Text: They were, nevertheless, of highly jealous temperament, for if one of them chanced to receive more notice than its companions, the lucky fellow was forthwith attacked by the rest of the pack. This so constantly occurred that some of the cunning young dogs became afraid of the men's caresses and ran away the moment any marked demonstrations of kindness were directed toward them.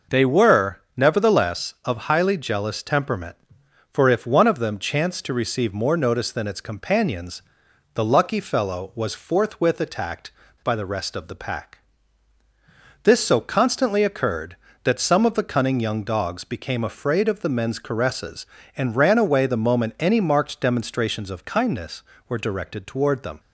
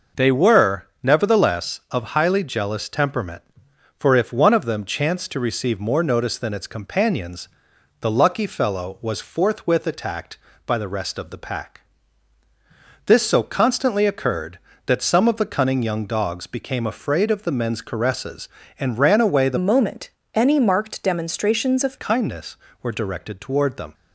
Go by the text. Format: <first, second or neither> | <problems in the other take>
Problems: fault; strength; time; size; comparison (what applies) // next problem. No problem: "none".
first | changes voice from "moment" to "of"; from 19.5 to 21.9 s; 2.4 s long // pauses between "moment" and "any"; slight; at 20.0 s; 0.24 s long